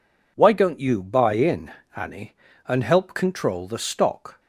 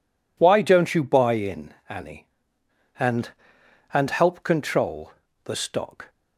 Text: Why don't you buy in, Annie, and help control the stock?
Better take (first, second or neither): first